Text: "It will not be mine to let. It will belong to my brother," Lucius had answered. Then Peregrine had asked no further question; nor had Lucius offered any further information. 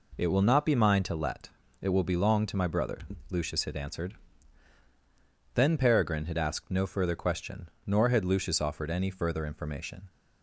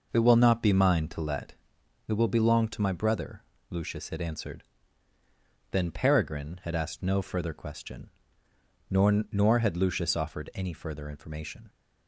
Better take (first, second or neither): first